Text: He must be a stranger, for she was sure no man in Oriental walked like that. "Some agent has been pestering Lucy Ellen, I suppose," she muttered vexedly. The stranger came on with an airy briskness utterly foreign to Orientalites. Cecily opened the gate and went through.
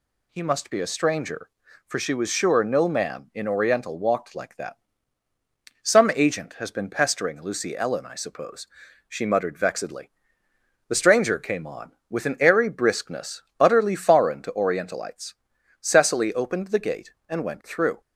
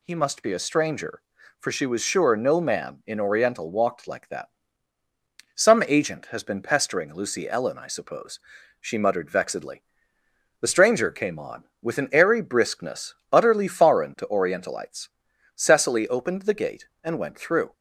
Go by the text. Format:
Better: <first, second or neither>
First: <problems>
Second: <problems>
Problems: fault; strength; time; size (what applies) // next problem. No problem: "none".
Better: neither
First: pauses between "briskness" and "utterly"; slight; at 13.4 s; 0.16 s long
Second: pauses between "briskness" and "utterly"; slight; at 13.1 s; 0.16 s long